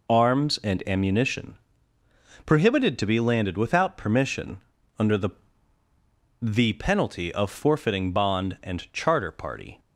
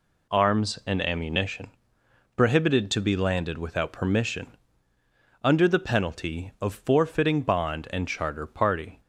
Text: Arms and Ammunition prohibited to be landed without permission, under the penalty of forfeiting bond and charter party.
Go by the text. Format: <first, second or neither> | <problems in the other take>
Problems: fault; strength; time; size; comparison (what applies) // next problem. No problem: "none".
second | pauses between "Ammunition" and "prohibited"; noticeable; at 1.5 s; 0.90 s long; noticeable in the second // says "the" twice; at 6.4 s